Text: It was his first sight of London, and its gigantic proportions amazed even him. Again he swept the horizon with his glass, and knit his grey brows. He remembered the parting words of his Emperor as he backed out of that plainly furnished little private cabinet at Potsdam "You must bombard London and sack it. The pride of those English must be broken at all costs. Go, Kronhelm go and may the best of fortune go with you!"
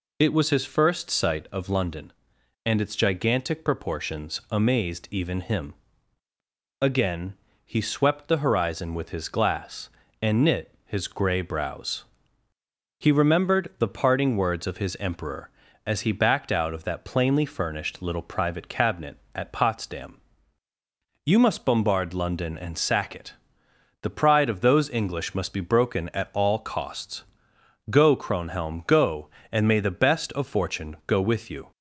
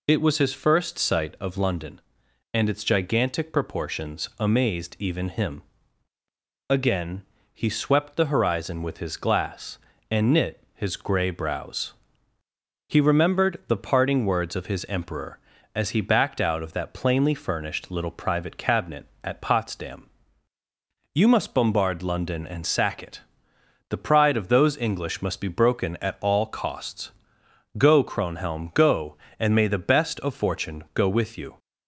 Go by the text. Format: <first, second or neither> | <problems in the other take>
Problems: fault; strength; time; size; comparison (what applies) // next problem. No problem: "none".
neither | pauses between "Again" and "he"; slight; the same in both // pauses between "Potsdam" and "You"; the same in both